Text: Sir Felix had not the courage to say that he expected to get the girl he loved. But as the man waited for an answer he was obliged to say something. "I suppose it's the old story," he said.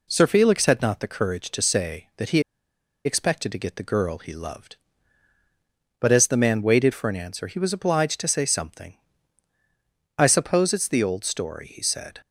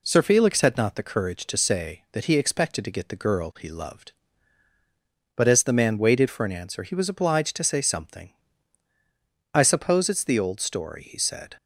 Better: second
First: pauses between "he" and "expected"; noticeable; at 2.4 s; 0.63 s long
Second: none

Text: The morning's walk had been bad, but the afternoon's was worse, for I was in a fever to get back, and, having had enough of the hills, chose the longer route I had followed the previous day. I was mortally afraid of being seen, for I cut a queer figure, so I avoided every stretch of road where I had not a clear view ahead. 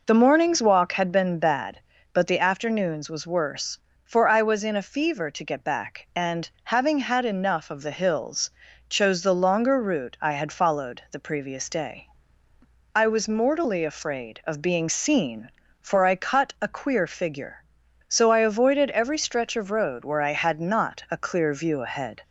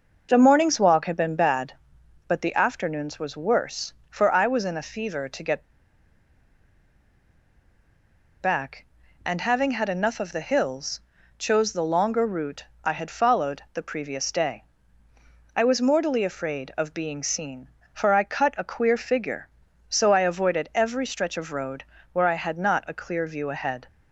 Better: first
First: none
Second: pauses between "get" and "back"; strong; at 5.6 s; 2.7 s long // pauses between "route" and "I"; slight; at 12.6 s; 0.18 s long // pauses between "road" and "where"; slight; at 21.8 s; 0.26 s long

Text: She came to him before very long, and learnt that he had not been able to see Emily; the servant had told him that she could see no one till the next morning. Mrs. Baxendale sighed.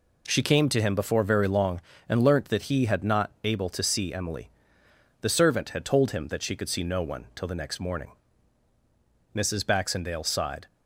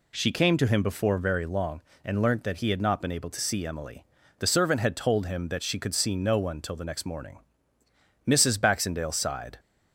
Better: second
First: skips "been"; at 3.3 s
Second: none

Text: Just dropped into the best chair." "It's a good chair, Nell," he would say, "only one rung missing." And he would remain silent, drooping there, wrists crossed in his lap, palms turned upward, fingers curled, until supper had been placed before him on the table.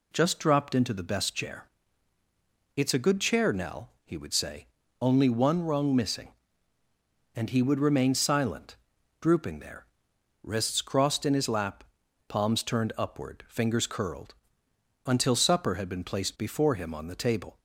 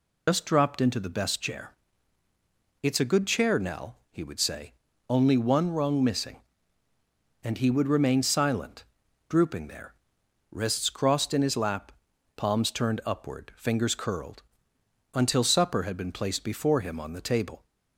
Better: first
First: none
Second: loses the start of "Just"; at 0.2 s; 90 ms

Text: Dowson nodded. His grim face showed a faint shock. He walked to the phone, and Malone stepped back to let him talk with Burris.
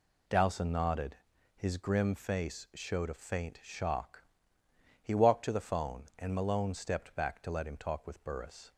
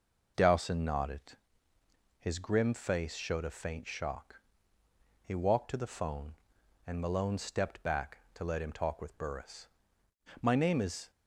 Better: first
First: none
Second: goes on to say "My name is"; noticeable; from 10.4 s on; 0.70 s long

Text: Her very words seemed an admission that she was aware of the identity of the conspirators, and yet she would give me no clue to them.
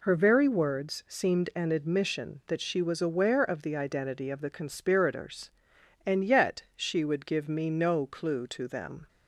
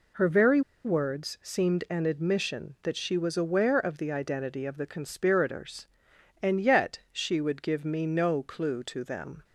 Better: first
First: none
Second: pauses between "very" and "words"; slight; at 0.6 s; 0.24 s long

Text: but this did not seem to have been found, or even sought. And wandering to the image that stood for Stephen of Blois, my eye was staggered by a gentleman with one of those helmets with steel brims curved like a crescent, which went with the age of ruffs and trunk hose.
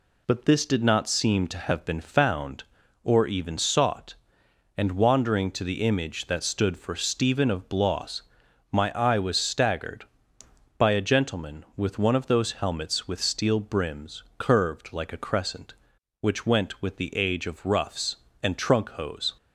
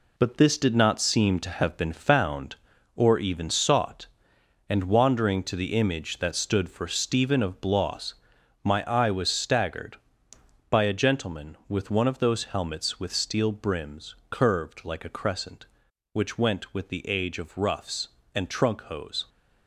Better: first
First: pauses between "brims" and "curved"; slight; at 14.2 s; 0.16 s long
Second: gets quieter; strong; throughout; 8 dB // pauses between "brims" and "curved"; slight; at 14.1 s; 0.16 s long

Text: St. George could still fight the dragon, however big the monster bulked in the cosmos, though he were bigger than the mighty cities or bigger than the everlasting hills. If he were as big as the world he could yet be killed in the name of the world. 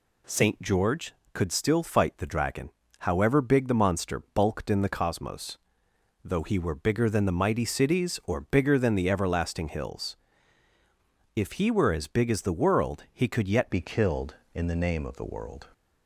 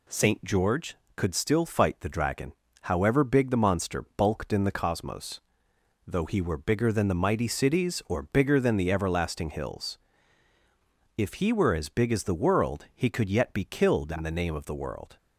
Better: second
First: changes voice at "be"; from 13.6 s on; 2.0 s long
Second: none

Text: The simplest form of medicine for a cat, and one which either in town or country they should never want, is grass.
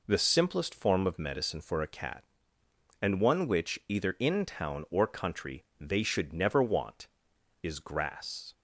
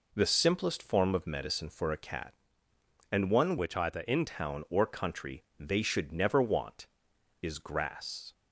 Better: first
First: pauses between "country" and "they"; slight; at 5.6 s; 0.16 s long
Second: changes voice from "which" to "in"; from 3.5 to 4.2 s; 0.7 s long // pauses between "country" and "they"; slight; at 5.4 s; 0.16 s long

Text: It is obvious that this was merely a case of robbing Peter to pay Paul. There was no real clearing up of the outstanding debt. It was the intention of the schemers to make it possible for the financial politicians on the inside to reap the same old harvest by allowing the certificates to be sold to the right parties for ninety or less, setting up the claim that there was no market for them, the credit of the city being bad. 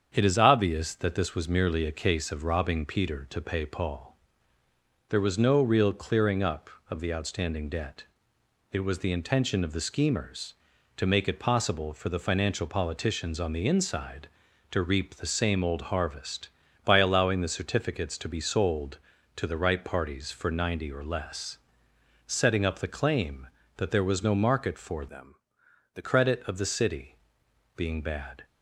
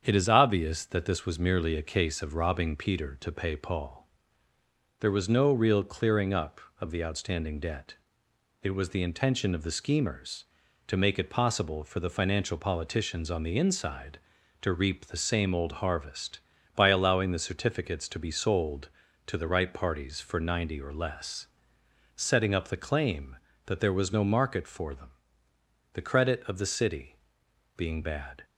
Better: second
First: starts louder than the rest; strong; until 1.1 s; 7.5 dB // changes voice from "them" to "the"; from 25.0 to 26.0 s; 1.0 s long // pauses between "city" and "being"; noticeable; at 27.1 s; 0.60 s long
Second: starts louder than the rest; strong; until 1.0 s; 7.5 dB // pauses between "city" and "being"; noticeable; at 27.1 s; 0.60 s long

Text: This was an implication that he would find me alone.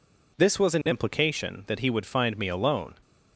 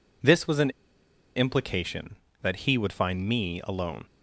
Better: first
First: none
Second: pauses between "an" and "implication"; noticeable; at 0.6 s; 0.65 s long

